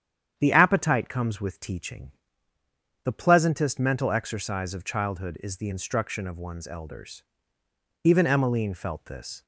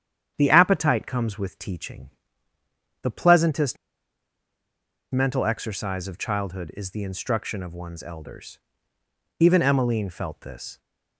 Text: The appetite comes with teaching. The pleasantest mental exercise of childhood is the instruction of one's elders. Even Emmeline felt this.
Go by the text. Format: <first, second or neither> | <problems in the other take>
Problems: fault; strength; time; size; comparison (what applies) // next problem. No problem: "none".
first | starts louder than the rest; strong; until 1.3 s; 9 dB; strong in the first // pauses between "pleasantest" and "mental"; strong; at 3.7 s; 1.3 s long